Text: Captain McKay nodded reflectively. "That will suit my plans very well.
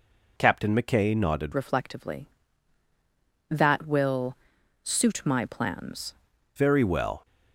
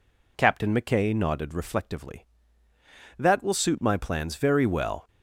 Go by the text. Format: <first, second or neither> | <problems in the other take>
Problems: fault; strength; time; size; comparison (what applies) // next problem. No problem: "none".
second | changes voice from "reflectively" to "plans"; from 1.5 to 6.1 s; 4.6 s long // pauses between "will" and "suit"; noticeable; at 4.3 s; 0.46 s long